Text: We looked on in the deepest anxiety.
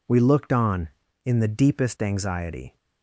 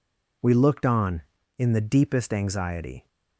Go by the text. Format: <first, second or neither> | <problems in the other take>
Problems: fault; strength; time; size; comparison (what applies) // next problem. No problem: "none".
neither | none